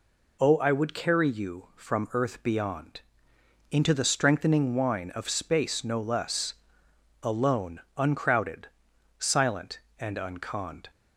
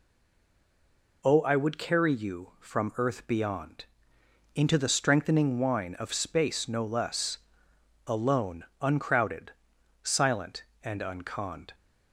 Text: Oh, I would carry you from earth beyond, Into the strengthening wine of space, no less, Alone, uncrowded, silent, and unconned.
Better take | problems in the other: first | stays silent before the first word; noticeable; until 1.2 s; 1.2 s long

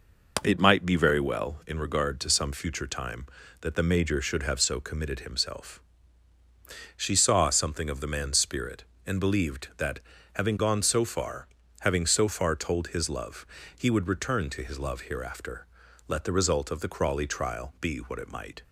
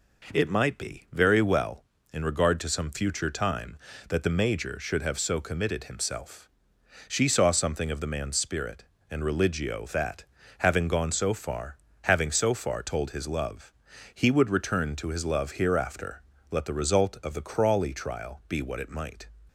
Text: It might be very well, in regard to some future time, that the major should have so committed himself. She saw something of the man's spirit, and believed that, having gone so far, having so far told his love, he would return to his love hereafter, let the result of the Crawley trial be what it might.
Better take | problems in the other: first | says "religio" for "believed"; at 9.2 s

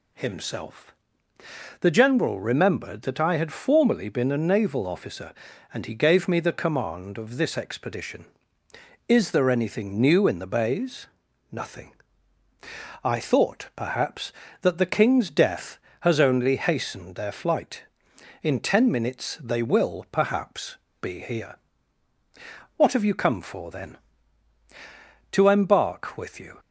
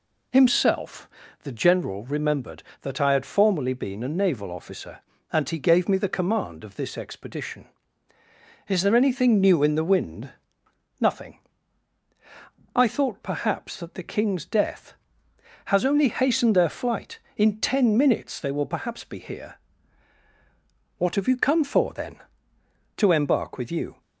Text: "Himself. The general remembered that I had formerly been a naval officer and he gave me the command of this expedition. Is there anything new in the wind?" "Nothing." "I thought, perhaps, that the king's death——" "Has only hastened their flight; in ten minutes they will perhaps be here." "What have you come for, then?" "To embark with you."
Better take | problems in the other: second | says "bays" for "wind"; at 10.4 s // pauses between "perhaps" and "be"; slight; at 20.7 s; 0.26 s long

